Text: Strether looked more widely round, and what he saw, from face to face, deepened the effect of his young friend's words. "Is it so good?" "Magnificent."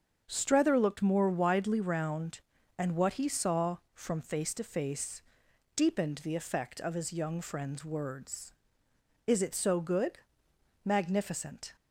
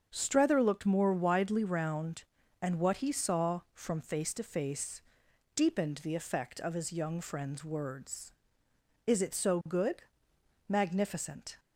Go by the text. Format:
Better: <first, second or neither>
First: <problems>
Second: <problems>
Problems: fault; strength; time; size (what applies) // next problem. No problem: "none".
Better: neither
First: starts louder than the rest; until 1.2 s; 7 dB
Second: starts louder than the rest; until 1.1 s; 7 dB